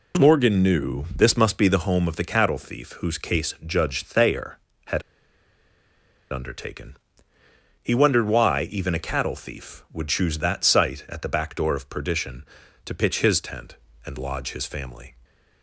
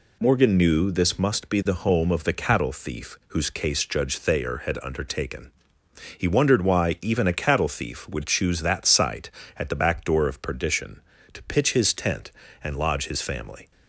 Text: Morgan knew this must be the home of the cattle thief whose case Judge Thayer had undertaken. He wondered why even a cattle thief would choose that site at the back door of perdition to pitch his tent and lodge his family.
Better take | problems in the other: second | pauses between "had" and "undertaken"; strong; at 5.0 s; 1.3 s long

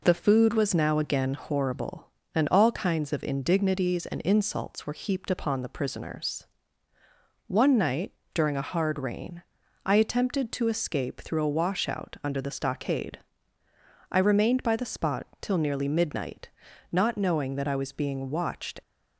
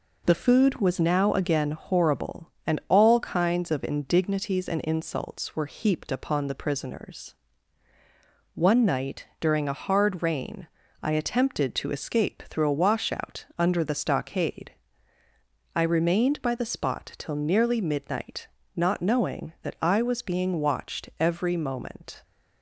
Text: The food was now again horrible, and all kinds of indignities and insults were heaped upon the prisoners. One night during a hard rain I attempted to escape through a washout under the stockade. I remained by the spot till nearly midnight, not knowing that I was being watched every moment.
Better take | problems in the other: second | pauses between "night" and "during"; slight; at 8.1 s; 0.22 s long // pauses between "rain" and "I"; at 9.4 s; 0.42 s long; slight in the second // stops before "every moment"; at 18.8 s

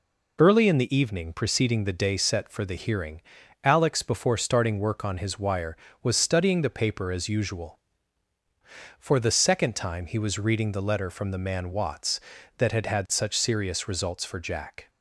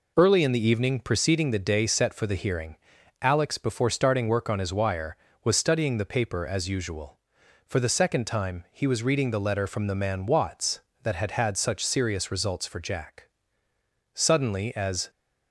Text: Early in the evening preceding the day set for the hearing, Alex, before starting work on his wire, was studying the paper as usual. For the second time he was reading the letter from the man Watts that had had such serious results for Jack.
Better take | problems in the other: first | goes on to say "Suddenly as"; noticeable; from 14.1 s on; 0.96 s long

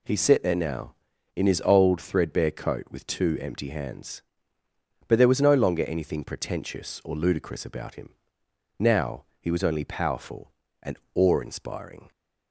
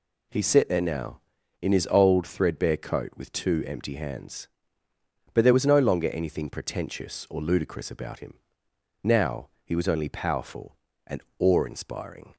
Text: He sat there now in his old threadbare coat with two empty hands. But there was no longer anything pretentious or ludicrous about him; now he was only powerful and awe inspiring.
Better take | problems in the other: neither | pauses between "and" and "awe"; slight; the same in both

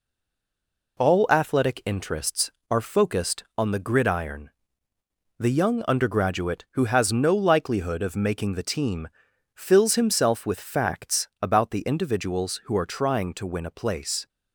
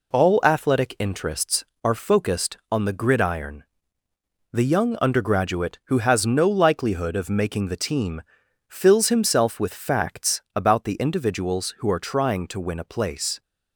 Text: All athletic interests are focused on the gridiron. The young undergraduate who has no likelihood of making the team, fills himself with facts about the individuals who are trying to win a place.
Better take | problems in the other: second | stays silent before the first word; until 0.9 s; 0.9 s long

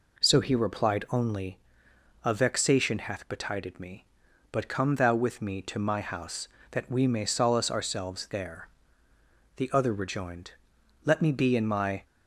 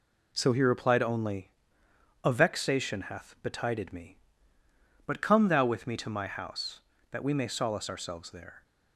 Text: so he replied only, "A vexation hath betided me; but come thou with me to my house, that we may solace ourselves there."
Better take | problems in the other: second | goes on to say "The other rejoined Let me be in my"; strong; from 9.5 s on; 2.4 s long

